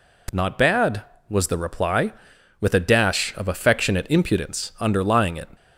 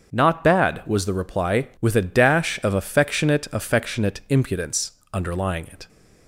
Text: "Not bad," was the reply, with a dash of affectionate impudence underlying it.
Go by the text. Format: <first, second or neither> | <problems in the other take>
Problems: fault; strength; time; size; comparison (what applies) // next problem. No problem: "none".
first | starts louder than the rest; until 1.1 s; 6.5 dB // says "affectionate" twice; at 3.5 s // pauses between "impudence" and "underlying"; slight; at 4.9 s; 0.20 s long